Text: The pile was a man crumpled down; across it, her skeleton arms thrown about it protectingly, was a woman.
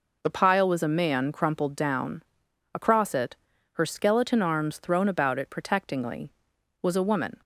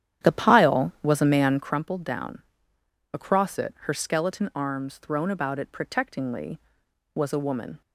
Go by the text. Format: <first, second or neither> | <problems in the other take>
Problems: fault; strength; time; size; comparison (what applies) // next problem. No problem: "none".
first | starts louder than the rest; strong; until 1.8 s; 10.5 dB